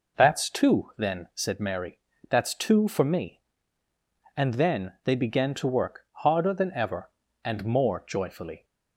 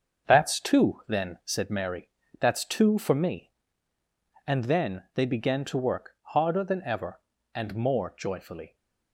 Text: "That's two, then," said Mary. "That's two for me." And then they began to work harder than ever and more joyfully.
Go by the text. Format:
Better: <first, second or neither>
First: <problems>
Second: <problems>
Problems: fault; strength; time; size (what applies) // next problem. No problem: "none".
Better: first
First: none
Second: gets quieter; strong; throughout; 7 dB